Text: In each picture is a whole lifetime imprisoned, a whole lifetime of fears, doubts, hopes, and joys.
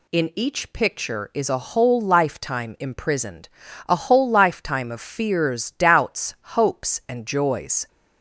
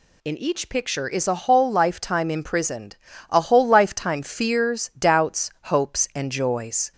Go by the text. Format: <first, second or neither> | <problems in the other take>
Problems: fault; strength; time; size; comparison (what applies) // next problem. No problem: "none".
first | skips "of"; at 4.2 s